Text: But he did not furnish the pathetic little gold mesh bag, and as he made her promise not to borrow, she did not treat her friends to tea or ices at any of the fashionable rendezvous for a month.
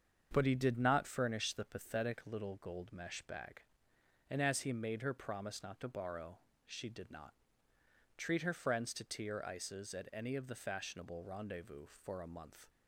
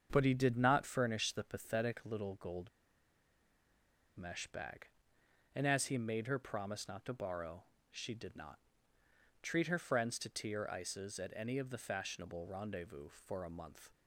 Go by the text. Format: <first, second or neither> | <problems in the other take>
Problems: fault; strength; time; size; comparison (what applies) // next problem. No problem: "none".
first | starts louder than the rest; until 1.1 s; 7 dB; also in the first // pauses between "gold" and "mesh"; strong; at 2.6 s; 1.4 s long // pauses between "not" and "treat"; noticeable; at 8.5 s; 0.82 s long; noticeable in the first